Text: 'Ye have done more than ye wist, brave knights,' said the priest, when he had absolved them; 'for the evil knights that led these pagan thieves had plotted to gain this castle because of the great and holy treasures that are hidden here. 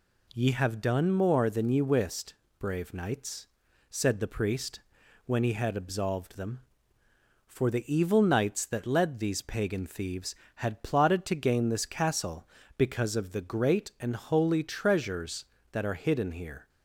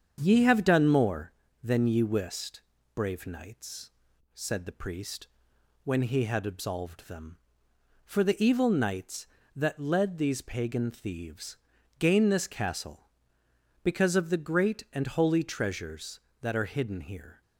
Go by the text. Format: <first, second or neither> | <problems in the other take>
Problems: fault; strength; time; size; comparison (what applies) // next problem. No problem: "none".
first | starts louder than the rest; strong; until 1.2 s; 7.5 dB // skips "had plotted to"; at 11.7 s